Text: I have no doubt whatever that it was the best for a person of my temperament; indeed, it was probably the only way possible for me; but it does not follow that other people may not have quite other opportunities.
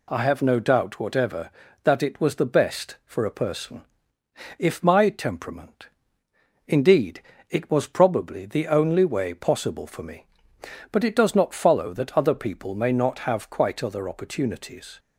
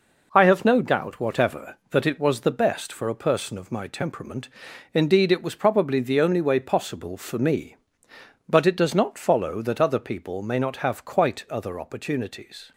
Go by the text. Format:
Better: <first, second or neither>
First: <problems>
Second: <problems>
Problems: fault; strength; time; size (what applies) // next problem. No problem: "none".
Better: second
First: says "if" for "of"; at 4.5 s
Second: none